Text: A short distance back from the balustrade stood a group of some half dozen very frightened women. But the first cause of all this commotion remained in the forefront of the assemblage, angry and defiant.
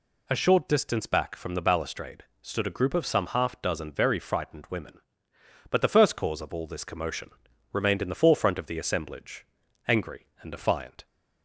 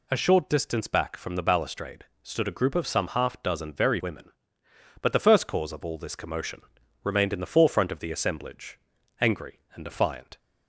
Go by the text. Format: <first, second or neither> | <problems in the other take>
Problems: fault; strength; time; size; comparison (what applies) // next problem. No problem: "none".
first | pauses between "balustrade" and "stood"; slight; at 2.0 s; 0.18 s long; slight in the first // skips "frightened"; at 4.0 s // pauses between "commotion" and "remained"; at 6.6 s; 0.42 s long; also in the first